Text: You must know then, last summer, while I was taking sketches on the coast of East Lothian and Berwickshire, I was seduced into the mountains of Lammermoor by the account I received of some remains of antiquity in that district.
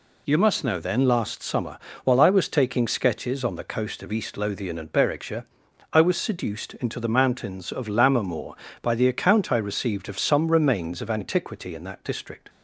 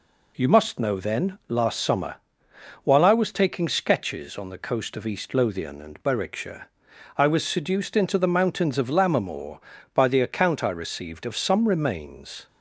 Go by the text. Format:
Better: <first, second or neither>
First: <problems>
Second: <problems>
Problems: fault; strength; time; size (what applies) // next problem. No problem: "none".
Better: first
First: none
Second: stops before "of antiquity in that district"; at 12.4 s